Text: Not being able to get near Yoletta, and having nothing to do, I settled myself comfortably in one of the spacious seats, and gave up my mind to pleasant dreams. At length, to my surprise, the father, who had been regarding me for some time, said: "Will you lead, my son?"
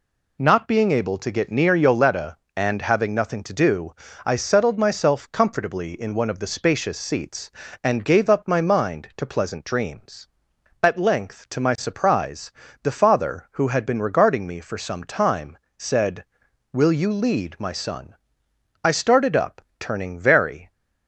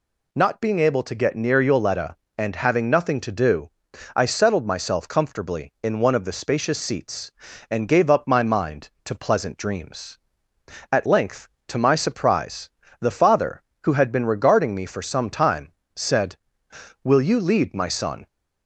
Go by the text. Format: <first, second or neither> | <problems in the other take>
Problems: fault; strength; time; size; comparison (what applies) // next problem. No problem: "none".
second | goes on to say "I started up turning very"; strong; from 18.8 s on; 1.8 s long